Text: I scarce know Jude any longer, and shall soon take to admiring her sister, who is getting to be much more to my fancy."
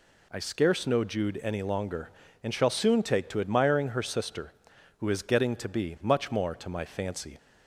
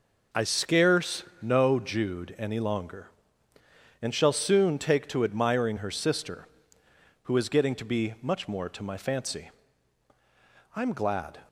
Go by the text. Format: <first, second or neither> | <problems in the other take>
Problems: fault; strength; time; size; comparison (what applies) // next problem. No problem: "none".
first | pauses between "scarce" and "know"; slight; at 1.2 s; 0.18 s long // goes on to say "I'm glad"; noticeable; from 10.7 s on; 0.64 s long